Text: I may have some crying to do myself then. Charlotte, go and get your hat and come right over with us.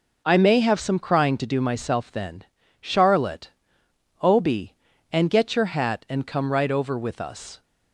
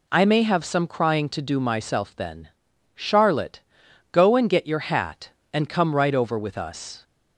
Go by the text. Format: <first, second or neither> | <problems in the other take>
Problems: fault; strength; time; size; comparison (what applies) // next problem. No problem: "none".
second | says "obi" for "go"; at 4.2 s